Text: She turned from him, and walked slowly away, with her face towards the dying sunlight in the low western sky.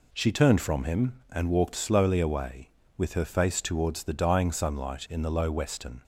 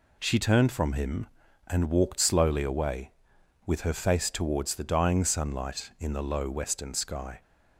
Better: second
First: stops before "sky"; at 6.0 s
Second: none

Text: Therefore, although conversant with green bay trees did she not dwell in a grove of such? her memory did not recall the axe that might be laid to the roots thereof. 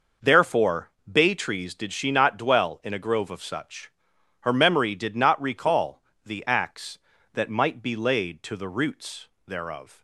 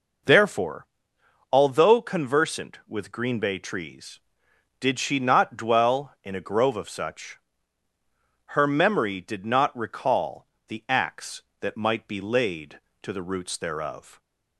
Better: second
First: skips "although conversant with green"; at 0.9 s // pauses between "recall" and "the"; slight; at 6.0 s; 0.22 s long // pauses between "roots" and "thereof"; slight; at 9.2 s; 0.18 s long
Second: pauses between "recall" and "the"; slight; at 10.4 s; 0.22 s long

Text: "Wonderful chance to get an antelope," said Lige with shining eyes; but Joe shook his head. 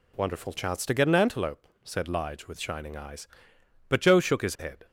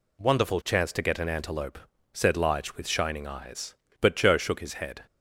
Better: neither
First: none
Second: none

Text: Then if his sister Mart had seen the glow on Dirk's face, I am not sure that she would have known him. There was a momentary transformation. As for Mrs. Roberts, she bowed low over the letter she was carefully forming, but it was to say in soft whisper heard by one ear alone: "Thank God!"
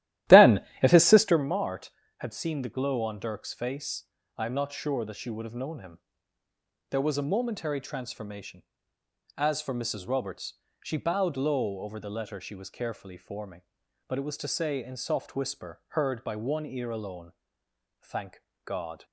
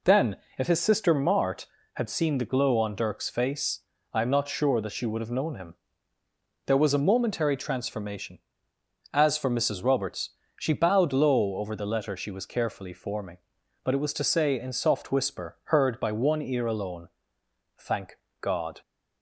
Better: second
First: starts louder than the rest; strong; until 1.5 s; 14.5 dB // pauses between "Then" and "if"; slight; at 0.6 s; 0.20 s long // pauses between "Thank" and "God"; slight; at 18.4 s; 0.24 s long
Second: pauses between "Then" and "if"; slight; at 0.3 s; 0.20 s long // pauses between "Thank" and "God"; slight; at 18.1 s; 0.24 s long

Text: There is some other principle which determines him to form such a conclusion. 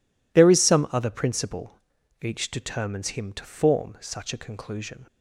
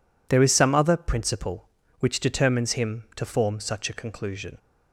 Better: second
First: says "each" for "which"; at 2.2 s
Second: none

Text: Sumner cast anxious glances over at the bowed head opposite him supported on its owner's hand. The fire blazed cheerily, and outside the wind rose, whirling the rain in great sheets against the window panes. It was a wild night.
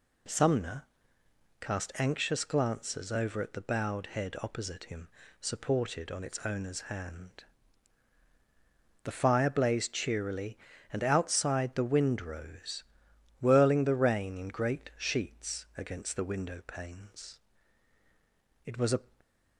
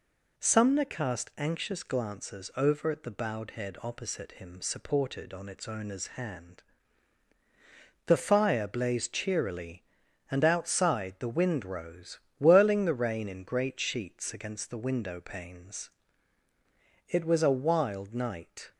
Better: second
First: pauses between "Sumner" and "cast"; noticeable; at 0.8 s; 0.78 s long // pauses between "him" and "supported"; slight; at 5.0 s; 0.34 s long // stops before "wild night"; at 19.2 s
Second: none

